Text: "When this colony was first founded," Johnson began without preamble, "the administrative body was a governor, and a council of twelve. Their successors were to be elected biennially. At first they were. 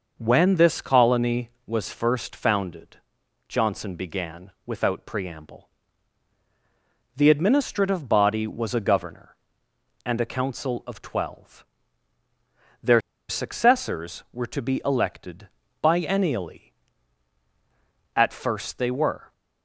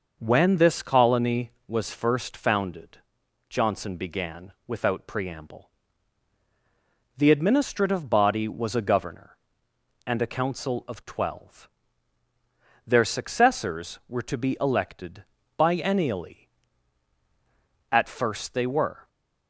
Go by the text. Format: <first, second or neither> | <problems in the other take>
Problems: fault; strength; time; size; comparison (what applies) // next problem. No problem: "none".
second | pauses between "began" and "without"; slight; at 4.4 s; 0.16 s long; slight in the second // pauses between "Their" and "successors"; slight; at 12.9 s; 0.29 s long // pauses between "elected" and "biennially"; slight; at 15.4 s; 0.34 s long; slight in the second